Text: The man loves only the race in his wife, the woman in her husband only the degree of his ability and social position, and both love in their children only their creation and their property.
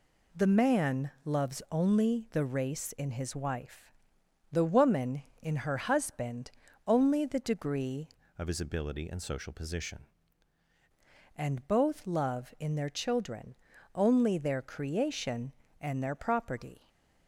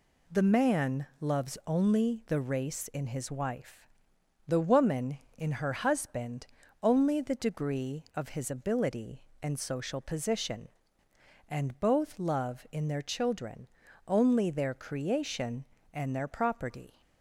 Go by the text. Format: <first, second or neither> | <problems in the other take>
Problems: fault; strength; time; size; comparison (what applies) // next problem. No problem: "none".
second | pauses between "husband" and "only"; slight; at 6.5 s; 0.36 s long; slight in the second // changes voice from "of" to "position"; from 8.3 to 10.0 s; 1.7 s long // pauses between "children" and "only"; at 13.5 s; 0.40 s long; also in the second